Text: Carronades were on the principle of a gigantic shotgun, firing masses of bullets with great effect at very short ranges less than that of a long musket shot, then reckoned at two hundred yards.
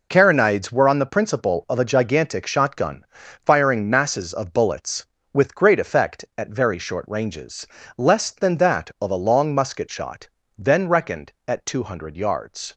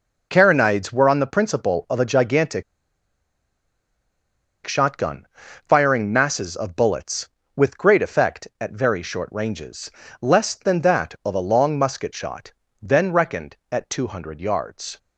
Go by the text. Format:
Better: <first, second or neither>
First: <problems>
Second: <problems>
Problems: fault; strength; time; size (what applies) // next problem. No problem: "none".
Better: first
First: pauses between "ranges" and "less"; slight; at 7.6 s; 0.28 s long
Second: pauses between "gigantic" and "shotgun"; strong; at 2.6 s; 2.0 s long // pauses between "ranges" and "less"; slight; at 9.9 s; 0.28 s long